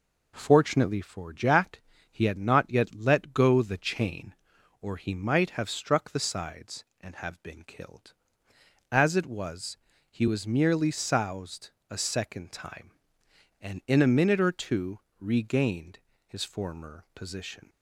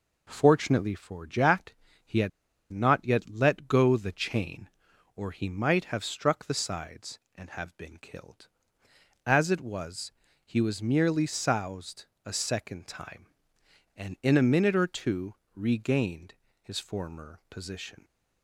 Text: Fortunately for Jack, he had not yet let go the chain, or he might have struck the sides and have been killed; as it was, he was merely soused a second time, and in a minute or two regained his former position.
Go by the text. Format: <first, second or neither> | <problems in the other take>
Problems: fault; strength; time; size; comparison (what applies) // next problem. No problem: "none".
first | pauses between "had" and "not"; at 2.3 s; 0.42 s long // pauses between "soused" and "a"; slight; at 12.0 s; 0.22 s long; slight in the first // pauses between "two" and "regained"; slight; at 15.3 s; 0.20 s long; slight in the first // pauses between "regained" and "his"; slight; at 16.3 s; 0.26 s long; slight in the first